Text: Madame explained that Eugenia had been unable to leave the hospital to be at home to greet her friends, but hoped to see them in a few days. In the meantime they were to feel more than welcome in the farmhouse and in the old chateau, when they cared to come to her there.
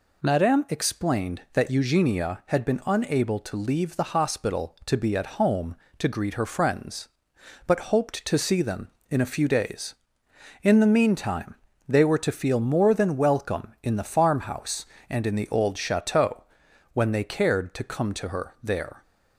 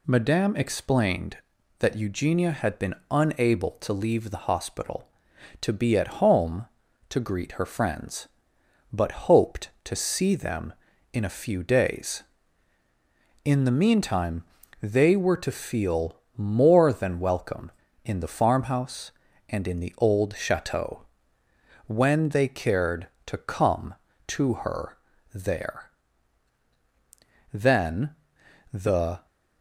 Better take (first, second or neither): first